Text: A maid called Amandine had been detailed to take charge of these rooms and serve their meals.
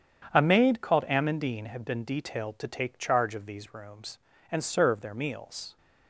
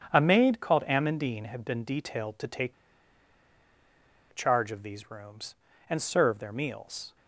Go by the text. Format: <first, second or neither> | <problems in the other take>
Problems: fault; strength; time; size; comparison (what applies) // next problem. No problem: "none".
first | starts louder than the rest; strong; until 1.1 s; 8 dB; strong in the first // pauses between "take" and "charge"; strong; at 2.7 s; 1.5 s long